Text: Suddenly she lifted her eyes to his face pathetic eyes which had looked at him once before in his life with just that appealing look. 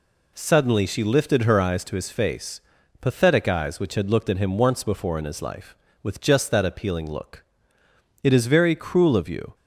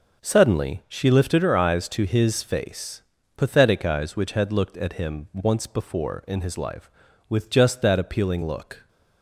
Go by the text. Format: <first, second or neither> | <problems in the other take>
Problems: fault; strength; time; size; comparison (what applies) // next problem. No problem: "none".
second | pauses between "face" and "pathetic"; at 2.6 s; 0.40 s long; slight in the second // goes on to say "It is very cruel of you"; from 8.2 s on; 1.3 s long